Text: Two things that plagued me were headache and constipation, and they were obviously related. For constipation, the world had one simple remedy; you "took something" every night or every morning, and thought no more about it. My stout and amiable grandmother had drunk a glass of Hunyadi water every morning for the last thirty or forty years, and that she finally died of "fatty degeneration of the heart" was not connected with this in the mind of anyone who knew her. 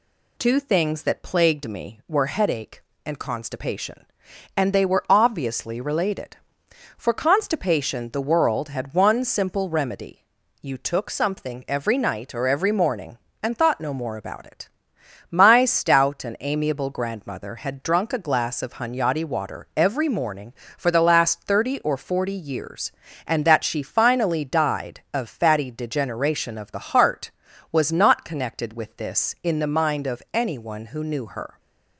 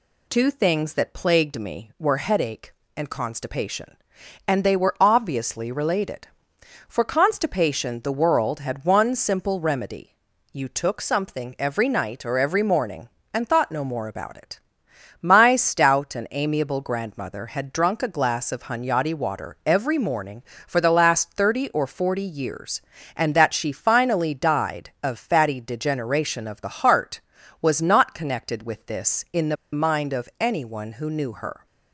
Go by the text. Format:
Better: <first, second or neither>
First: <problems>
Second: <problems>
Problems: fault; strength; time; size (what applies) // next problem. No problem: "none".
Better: first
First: none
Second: pauses between "the" and "mind"; slight; at 29.5 s; 0.17 s long